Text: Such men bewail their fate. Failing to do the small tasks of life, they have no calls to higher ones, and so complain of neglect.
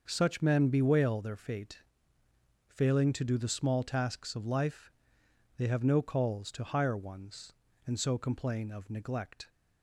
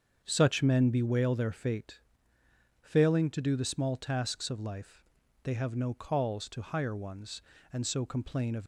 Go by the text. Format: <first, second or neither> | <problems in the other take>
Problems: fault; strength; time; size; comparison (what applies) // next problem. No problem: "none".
first | starts louder than the rest; until 1.2 s; 7 dB; noticeable in the first // stops before "neglect"; at 8.6 s